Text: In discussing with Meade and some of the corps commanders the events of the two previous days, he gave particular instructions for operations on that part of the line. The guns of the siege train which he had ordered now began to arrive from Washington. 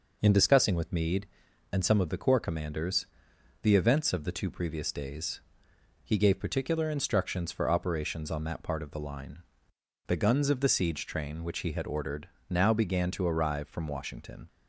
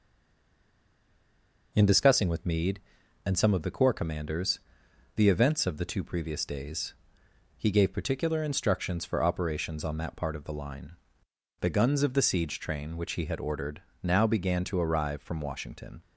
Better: first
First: pauses between "commanders" and "the"; noticeable; at 3.0 s; 0.58 s long // pauses between "ordered" and "now"; slight; at 12.2 s; 0.20 s long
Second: stays silent before the first word; noticeable; until 1.7 s; 1.7 s long // pauses between "commanders" and "the"; noticeable; at 4.5 s; 0.58 s long // pauses between "ordered" and "now"; slight; at 13.8 s; 0.20 s long

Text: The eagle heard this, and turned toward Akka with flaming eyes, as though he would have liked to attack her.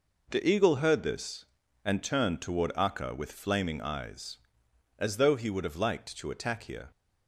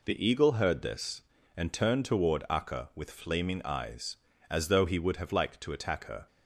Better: second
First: says "here" for "her"; at 6.6 s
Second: none

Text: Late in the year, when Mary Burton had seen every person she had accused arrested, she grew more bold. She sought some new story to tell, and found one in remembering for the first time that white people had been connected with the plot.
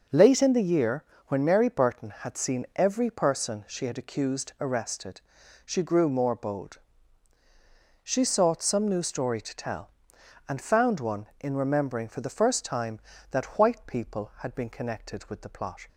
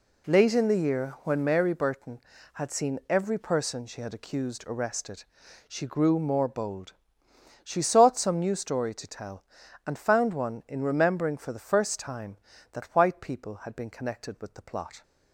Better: neither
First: none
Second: none

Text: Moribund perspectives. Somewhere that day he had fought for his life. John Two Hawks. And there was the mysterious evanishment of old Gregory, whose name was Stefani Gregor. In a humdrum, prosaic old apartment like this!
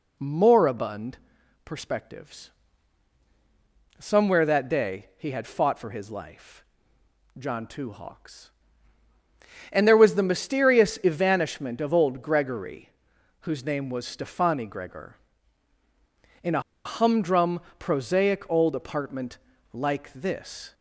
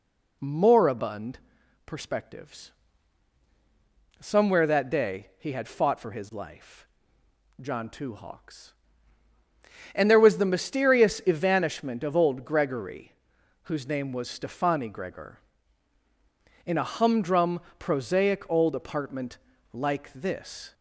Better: second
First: pauses between "Moribund" and "perspectives"; noticeable; at 1.1 s; 0.48 s long // pauses between "a" and "humdrum"; slight; at 16.6 s; 0.24 s long // pauses between "apartment" and "like"; slight; at 19.3 s; 0.36 s long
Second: pauses between "Moribund" and "perspectives"; noticeable; at 1.3 s; 0.48 s long // pauses between "apartment" and "like"; slight; at 19.3 s; 0.36 s long

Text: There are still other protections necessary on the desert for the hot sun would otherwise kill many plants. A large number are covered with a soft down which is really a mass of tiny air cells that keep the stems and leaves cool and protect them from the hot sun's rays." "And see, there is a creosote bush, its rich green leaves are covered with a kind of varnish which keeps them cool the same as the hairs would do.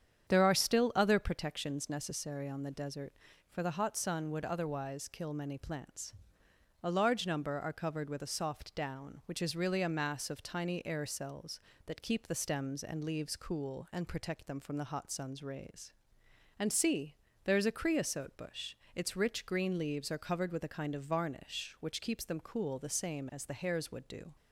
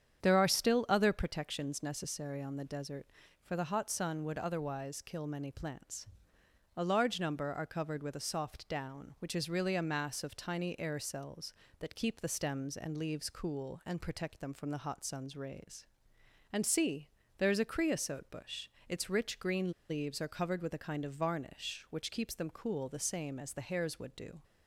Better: first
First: starts louder than the rest; strong; until 1.3 s; 8.5 dB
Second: starts louder than the rest; strong; until 1.2 s; 8.5 dB // pauses between "green" and "leaves"; slight; at 19.7 s; 0.17 s long

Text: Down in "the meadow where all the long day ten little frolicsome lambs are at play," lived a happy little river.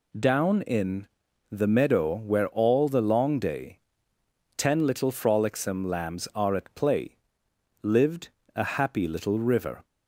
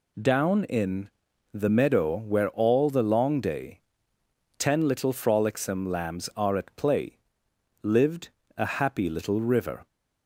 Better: neither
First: pauses between "in" and "the"; noticeable; at 1.0 s; 0.46 s long // pauses between "day" and "ten"; noticeable; at 3.7 s; 0.78 s long // pauses between "lived" and "a"; slight; at 8.2 s; 0.26 s long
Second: pauses between "in" and "the"; noticeable; at 1.0 s; 0.46 s long // pauses between "day" and "ten"; noticeable; at 3.7 s; 0.78 s long // pauses between "lived" and "a"; slight; at 8.2 s; 0.28 s long

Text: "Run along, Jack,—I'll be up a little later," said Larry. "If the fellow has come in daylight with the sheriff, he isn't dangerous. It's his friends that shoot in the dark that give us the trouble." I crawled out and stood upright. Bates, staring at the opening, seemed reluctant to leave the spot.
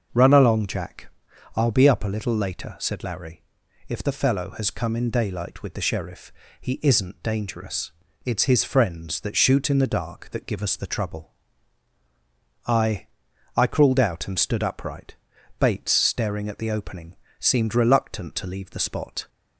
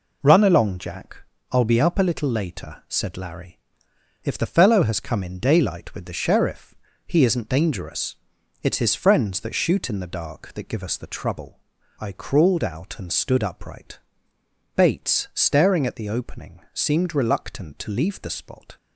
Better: second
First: starts louder than the rest; until 1.6 s; 6.5 dB // says "I" twice; at 13.5 s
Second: none

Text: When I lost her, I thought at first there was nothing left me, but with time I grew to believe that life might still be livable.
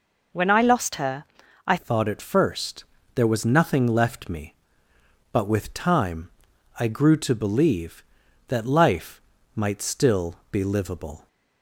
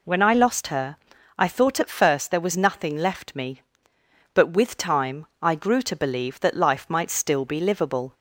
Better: second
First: changes voice at "thought"; from 1.7 s on; 9.5 s long // pauses between "first" and "there"; slight; at 2.8 s; 0.30 s long // pauses between "time" and "I"; noticeable; at 6.2 s; 0.50 s long // pauses between "life" and "might"; slight; at 9.2 s; 0.34 s long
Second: pauses between "time" and "I"; slight; at 5.2 s; 0.16 s long

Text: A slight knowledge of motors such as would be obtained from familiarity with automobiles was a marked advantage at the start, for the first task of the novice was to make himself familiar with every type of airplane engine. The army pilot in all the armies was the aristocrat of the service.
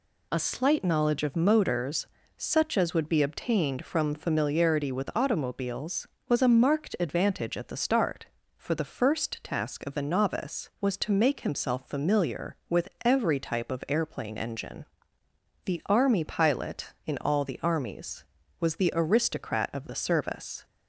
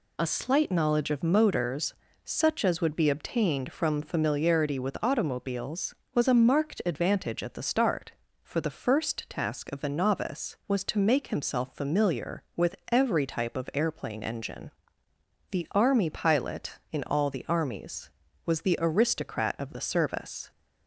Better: neither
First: pauses between "motors" and "such"; slight; at 2.0 s; 0.28 s long // pauses between "with" and "every"; slight; at 12.8 s; 0.16 s long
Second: pauses between "motors" and "such"; slight; at 1.9 s; 0.28 s long // pauses between "with" and "every"; slight; at 12.7 s; 0.16 s long

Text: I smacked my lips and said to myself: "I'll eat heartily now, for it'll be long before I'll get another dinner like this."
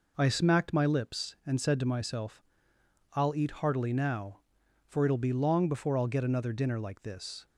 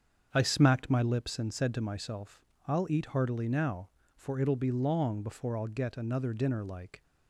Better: first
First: none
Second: starts louder than the rest; strong; until 1.3 s; 7 dB // stops before "this"; at 7.0 s

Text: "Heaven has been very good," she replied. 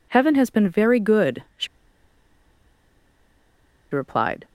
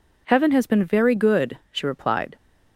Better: second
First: pauses between "she" and "replied"; strong; at 1.6 s; 2.2 s long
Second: none

